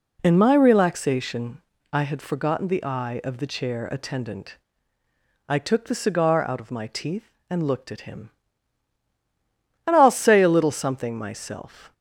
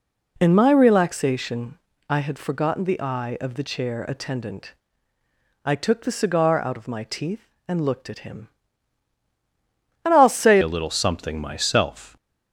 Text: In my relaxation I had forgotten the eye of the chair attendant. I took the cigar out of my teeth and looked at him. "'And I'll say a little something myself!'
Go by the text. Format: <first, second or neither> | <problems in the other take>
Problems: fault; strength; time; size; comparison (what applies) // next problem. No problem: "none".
first | pauses between "relaxation" and "I"; slight; at 1.7 s; 0.32 s long; slight in the first // changes voice at "a"; from 10.6 s on; 1.5 s long